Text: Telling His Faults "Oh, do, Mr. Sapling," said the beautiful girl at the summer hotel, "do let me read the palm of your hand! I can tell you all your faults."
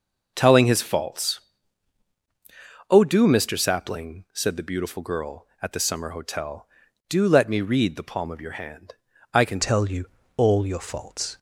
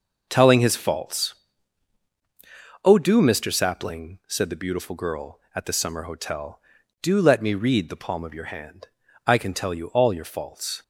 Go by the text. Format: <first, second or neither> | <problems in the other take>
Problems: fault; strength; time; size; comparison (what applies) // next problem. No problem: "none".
second | pauses between "Faults" and "Oh"; strong; at 1.3 s; 1.5 s long; strong in the second // changes voice at "tell"; from 9.6 s on; 1.7 s long // pauses between "you" and "all"; slight; at 10.0 s; 0.30 s long